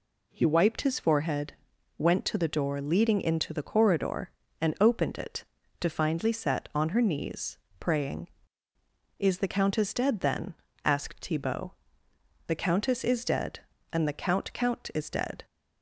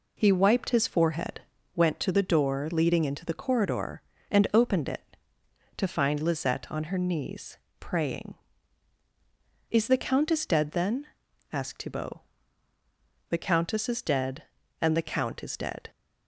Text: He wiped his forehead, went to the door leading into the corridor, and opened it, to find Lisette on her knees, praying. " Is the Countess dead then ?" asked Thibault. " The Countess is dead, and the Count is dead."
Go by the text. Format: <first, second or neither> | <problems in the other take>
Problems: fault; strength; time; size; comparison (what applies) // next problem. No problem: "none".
second | says "Count" twice; at 14.5 s